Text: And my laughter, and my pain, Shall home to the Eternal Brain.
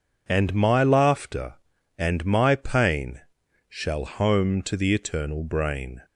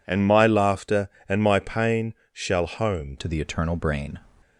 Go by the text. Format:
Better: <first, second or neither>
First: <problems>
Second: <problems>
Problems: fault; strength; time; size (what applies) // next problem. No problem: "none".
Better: first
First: none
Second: changes voice at "to"; from 3.1 s on; 1.1 s long